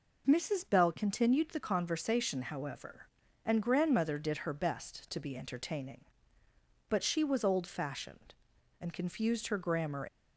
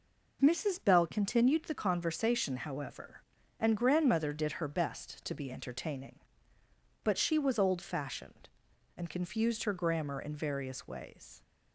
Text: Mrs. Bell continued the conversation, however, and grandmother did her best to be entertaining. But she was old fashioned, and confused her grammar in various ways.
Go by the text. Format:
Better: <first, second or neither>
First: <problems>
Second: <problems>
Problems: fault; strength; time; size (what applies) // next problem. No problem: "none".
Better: second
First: stops before "in various ways"; at 10.0 s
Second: none